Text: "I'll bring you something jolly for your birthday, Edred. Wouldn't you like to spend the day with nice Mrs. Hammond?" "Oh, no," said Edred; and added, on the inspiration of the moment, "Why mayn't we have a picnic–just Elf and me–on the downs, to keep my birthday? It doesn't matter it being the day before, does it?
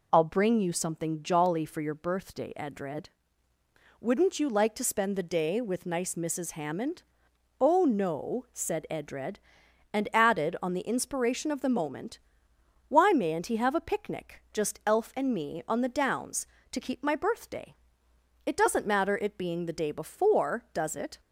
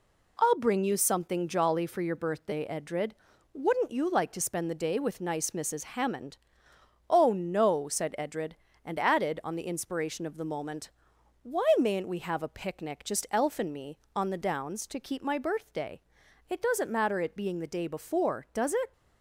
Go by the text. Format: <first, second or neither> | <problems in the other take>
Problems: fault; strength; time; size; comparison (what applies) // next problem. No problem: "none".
second | says "he" for "we"; at 13.4 s